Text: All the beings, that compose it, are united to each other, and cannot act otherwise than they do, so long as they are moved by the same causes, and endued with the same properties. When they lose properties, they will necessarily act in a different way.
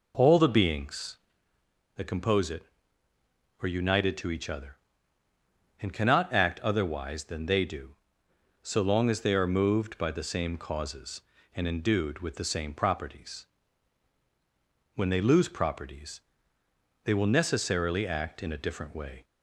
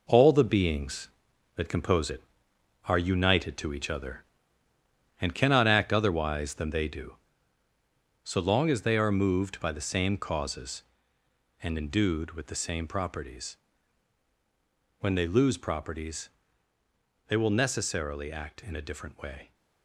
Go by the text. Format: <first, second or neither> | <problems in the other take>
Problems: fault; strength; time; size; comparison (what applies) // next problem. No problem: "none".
first | gets quieter; strong; throughout; 8 dB